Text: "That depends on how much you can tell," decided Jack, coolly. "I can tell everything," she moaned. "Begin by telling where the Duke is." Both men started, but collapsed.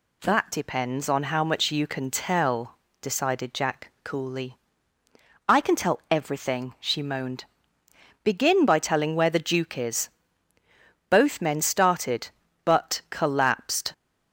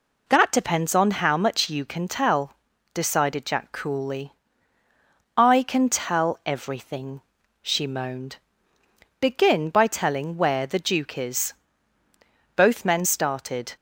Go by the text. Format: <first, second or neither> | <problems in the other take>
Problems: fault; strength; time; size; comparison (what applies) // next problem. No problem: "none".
first | stops before "but collapsed"; at 13.7 s